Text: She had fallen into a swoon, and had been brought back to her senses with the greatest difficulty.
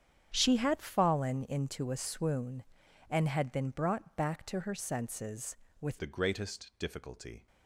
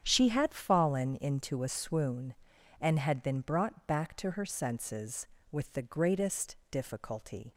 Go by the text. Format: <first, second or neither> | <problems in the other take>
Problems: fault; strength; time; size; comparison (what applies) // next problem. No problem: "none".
second | starts louder than the rest; strong; until 1.3 s; 8.5 dB; strong in the second // changes voice at "the"; from 5.9 s on; 1.5 s long